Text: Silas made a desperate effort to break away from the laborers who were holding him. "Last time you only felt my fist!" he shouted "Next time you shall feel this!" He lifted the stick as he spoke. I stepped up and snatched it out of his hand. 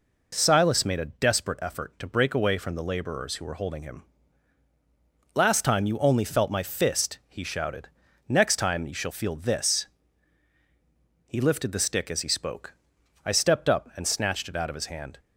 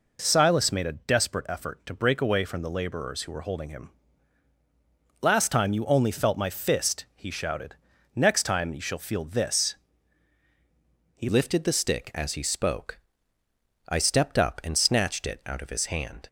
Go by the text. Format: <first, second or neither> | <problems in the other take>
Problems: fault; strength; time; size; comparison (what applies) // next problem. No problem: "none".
first | pauses between "shouted" and "Next"; at 7.7 s; 0.40 s long; also in the first // changes voice at "lifted"; from 11.2 s on; 5.0 s long